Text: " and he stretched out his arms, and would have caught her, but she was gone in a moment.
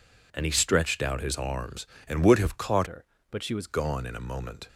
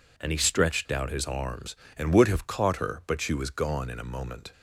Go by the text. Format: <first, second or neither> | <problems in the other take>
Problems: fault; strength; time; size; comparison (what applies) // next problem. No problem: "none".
second | changes voice from "her" to "was"; from 2.8 to 3.6 s; 0.8 s long